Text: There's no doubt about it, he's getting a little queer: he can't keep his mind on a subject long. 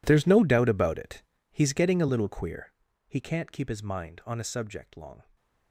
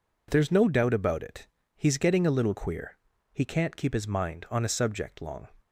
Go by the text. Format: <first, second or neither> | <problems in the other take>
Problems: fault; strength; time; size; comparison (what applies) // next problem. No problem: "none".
second | gets quieter; strong; throughout; 18.5 dB